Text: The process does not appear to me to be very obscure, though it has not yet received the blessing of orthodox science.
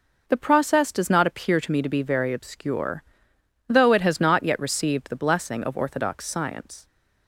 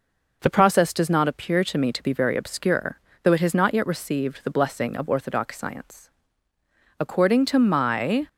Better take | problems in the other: first | goes on to say "According to my"; noticeable; from 6.9 s on; 1.2 s long

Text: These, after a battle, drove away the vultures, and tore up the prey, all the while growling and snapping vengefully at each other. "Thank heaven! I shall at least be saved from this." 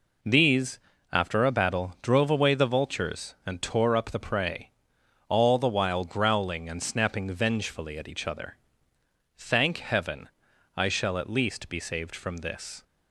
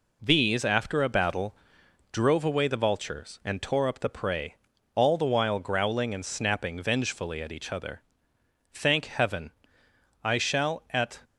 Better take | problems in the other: first | stops before "least be saved from this"; at 11.2 s

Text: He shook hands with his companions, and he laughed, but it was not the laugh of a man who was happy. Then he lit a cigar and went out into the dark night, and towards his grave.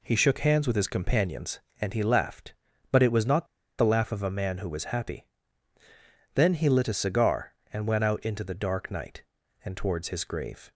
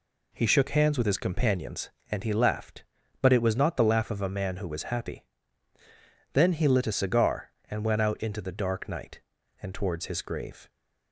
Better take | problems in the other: second | pauses between "not" and "the"; slight; at 3.4 s; 0.33 s long

